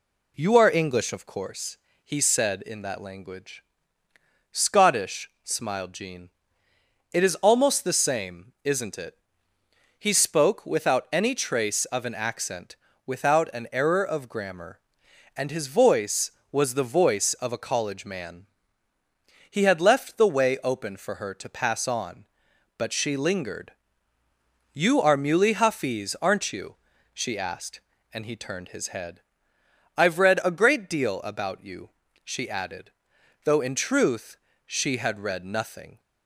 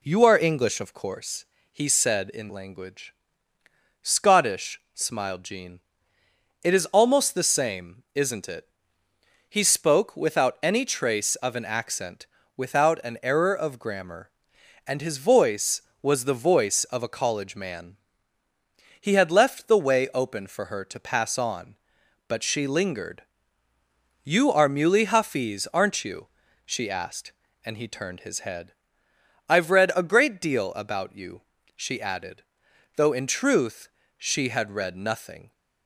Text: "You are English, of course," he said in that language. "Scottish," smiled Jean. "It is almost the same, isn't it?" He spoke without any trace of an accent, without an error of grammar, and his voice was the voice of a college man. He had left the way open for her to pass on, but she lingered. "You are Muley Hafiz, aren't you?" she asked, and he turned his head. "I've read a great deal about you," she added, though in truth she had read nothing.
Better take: first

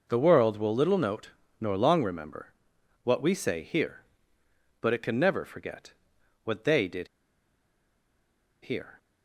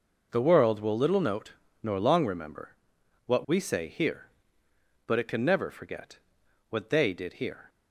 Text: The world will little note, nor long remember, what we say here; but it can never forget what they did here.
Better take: second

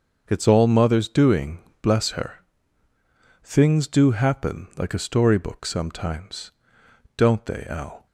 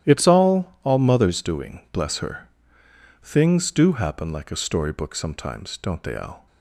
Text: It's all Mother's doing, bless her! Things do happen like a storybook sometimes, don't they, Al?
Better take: first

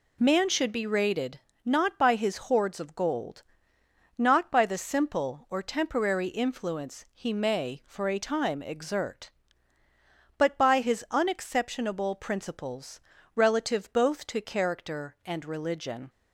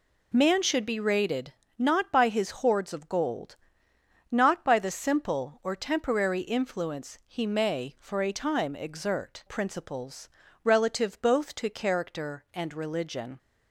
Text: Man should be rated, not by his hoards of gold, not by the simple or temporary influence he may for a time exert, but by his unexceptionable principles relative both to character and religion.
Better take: first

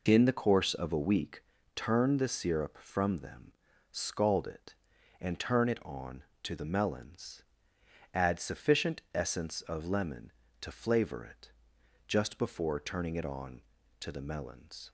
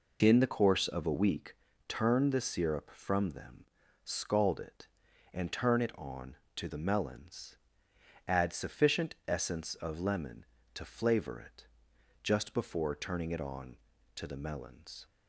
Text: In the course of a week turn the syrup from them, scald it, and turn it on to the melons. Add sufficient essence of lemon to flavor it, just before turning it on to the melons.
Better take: neither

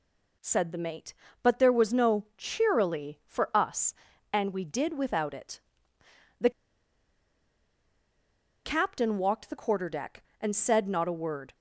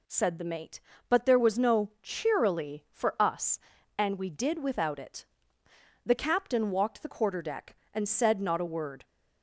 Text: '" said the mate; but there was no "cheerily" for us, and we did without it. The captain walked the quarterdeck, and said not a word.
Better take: second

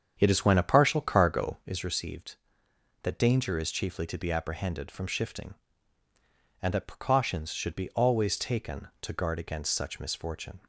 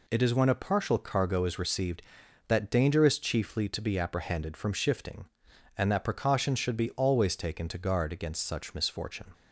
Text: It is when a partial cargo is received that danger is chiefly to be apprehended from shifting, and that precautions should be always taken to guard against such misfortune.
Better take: second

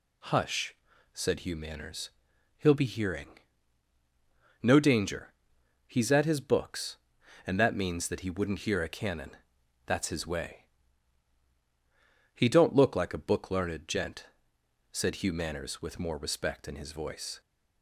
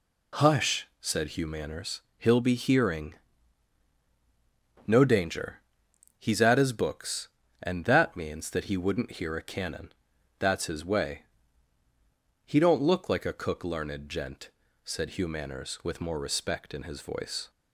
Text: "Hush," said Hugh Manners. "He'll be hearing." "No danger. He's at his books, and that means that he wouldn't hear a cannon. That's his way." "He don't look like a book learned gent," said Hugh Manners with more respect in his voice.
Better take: first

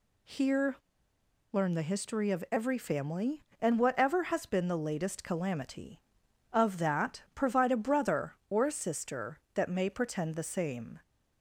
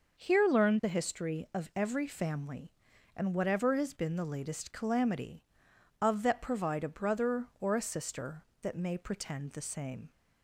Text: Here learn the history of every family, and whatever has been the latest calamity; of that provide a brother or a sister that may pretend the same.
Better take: second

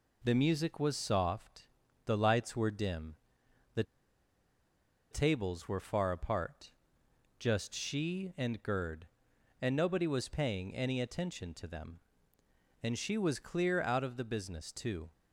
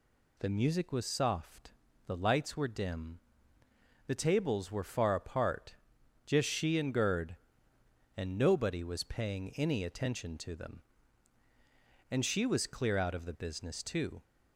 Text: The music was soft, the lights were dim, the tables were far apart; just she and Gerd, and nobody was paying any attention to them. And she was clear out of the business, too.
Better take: second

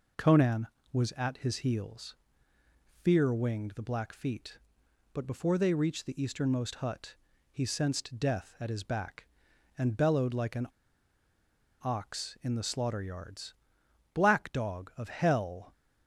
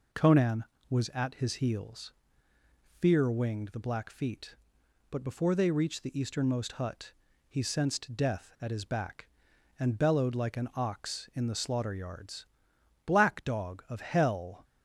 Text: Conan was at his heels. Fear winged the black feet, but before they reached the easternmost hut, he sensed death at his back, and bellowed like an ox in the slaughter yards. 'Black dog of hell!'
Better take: second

